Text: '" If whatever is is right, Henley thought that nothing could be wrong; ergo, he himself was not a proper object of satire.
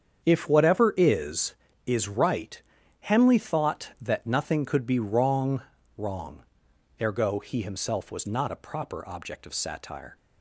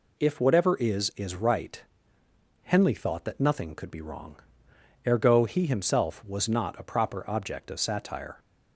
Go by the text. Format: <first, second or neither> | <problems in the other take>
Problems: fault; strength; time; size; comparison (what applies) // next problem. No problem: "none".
second | starts louder than the rest; strong; until 1.2 s; 7.5 dB // says "wrong" twice; at 5.9 s